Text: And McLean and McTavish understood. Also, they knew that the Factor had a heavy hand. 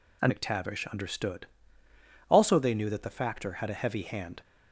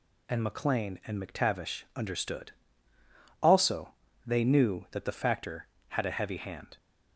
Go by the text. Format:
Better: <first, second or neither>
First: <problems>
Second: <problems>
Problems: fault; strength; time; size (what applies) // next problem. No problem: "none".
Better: second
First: skips "McLean and"; at 0.3 s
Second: none